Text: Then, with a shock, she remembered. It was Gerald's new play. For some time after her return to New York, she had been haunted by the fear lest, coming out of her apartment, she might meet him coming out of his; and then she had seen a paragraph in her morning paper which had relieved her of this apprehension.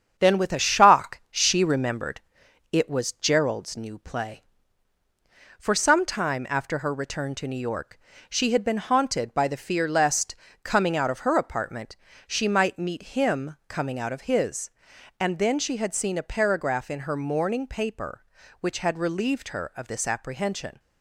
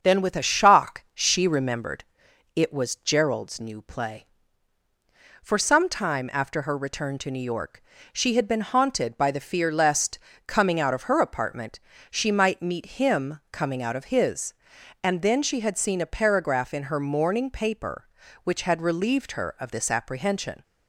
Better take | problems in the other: second | gets quieter; noticeable; throughout; 4 dB // starts louder than the rest; strong; until 1.1 s; 8 dB; also in the second

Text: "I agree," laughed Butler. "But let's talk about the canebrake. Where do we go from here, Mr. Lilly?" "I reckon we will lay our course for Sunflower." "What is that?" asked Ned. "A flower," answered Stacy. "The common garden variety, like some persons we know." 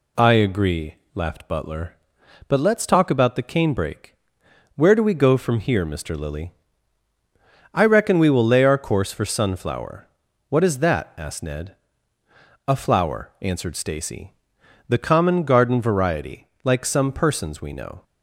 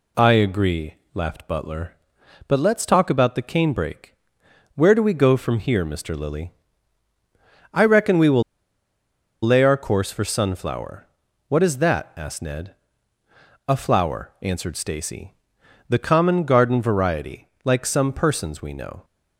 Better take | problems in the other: first | pauses between "will" and "lay"; at 8.4 s; 1.0 s long

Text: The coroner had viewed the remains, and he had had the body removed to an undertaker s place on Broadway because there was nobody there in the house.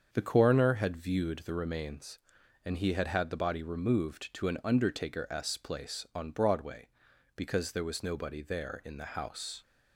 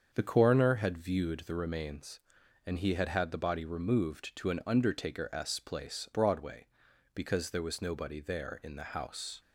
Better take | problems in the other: first | starts louder than the rest; until 1.1 s; 7 dB; also in the first // skips "on"; at 6.0 s

